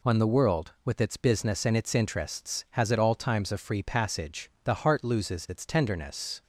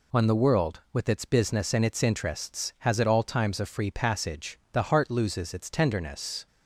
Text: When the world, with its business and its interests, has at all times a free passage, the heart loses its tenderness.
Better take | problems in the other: neither | none

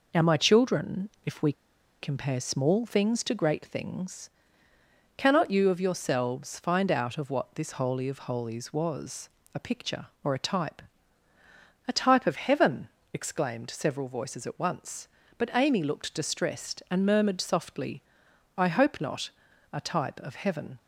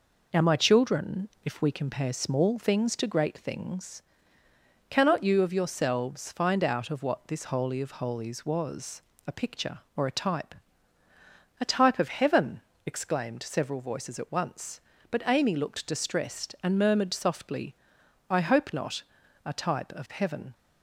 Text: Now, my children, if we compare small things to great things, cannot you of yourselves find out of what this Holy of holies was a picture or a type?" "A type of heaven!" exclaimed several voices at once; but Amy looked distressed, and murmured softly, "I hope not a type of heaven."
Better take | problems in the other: second | pauses between "we" and "compare"; noticeable; at 1.5 s; 0.49 s long // pauses between "was" and "a"; slight; at 9.2 s; 0.24 s long; slight in the second // pauses between "not" and "a"; noticeable; at 19.2 s; 0.46 s long; noticeable in the second

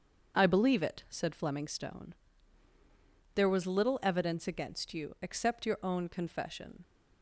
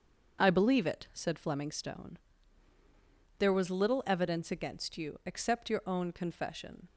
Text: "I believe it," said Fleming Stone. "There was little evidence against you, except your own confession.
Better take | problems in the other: neither | starts louder than the rest; the same in both

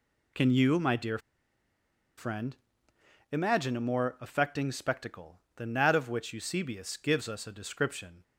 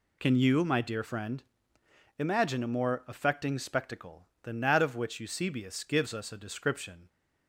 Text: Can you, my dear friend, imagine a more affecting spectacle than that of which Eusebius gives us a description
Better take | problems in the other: second | pauses between "dear" and "friend"; at 1.1 s; 0.99 s long

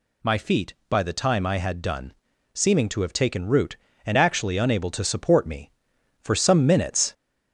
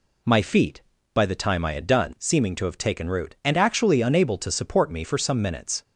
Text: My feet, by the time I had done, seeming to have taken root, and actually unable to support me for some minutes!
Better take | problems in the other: second | gets louder; slight; throughout; 3 dB

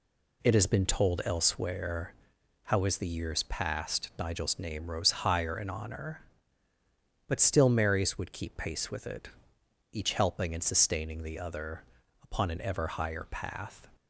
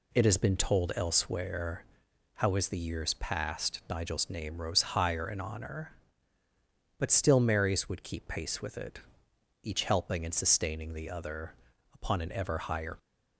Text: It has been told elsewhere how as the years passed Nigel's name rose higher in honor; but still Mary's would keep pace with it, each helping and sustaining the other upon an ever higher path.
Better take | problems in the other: first | pauses between "elsewhere" and "how"; noticeable; at 1.8 s; 0.48 s long; noticeable in the first // pauses between "other" and "upon"; at 11.5 s; 0.40 s long; also in the first // stops before "path"; at 12.9 s

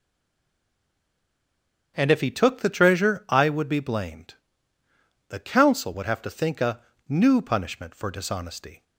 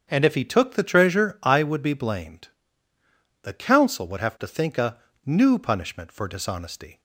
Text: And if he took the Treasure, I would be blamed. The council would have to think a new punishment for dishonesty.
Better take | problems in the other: second | stays silent before the first word; noticeable; until 1.9 s; 1.9 s long // starts louder than the rest; strong; until 2.9 s; 7.5 dB; strong in the second // pauses between "a" and "new"; slight; at 6.8 s; 0.26 s long; slight in the second

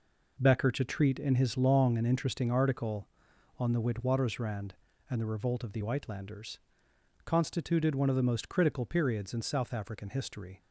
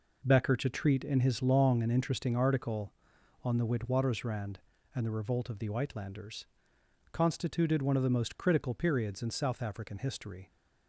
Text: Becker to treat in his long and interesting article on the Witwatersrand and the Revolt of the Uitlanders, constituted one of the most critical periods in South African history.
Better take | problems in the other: neither | none

